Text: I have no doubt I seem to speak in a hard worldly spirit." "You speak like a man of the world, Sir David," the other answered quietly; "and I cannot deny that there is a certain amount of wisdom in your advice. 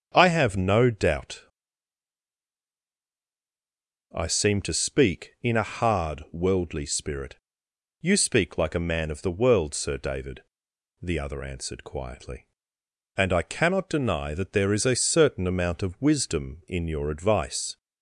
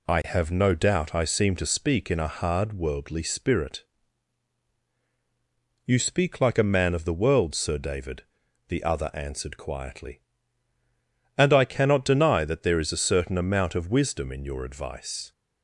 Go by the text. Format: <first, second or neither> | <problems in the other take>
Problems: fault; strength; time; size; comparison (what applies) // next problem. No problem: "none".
second | starts louder than the rest; strong; until 1.1 s; 8 dB // pauses between "doubt" and "I"; strong; at 1.4 s; 2.7 s long